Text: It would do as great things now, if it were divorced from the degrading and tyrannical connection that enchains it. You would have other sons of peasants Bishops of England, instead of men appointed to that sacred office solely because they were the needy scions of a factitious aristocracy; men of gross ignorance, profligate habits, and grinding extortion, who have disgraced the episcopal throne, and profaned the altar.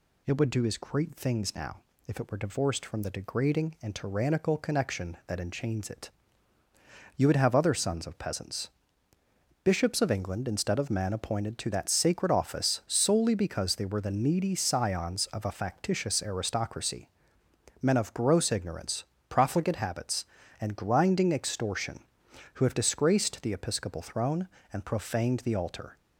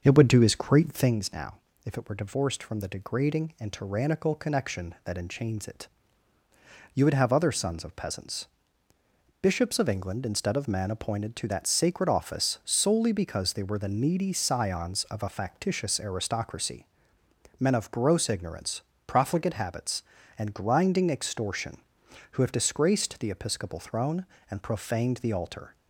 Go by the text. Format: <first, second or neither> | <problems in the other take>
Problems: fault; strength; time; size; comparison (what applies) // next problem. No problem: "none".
first | starts louder than the rest; until 1.2 s; 6 dB // pauses between "peasants" and "Bishops"; noticeable; at 8.4 s; 0.94 s long; noticeable in the first